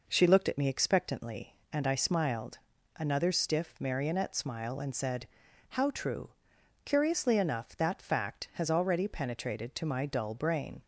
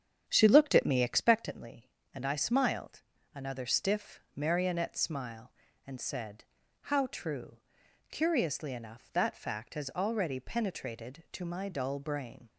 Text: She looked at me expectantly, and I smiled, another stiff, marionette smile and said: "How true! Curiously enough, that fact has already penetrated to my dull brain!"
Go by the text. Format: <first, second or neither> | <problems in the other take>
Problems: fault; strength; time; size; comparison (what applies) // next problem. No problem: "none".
first | starts louder than the rest; strong; until 1.3 s; 8 dB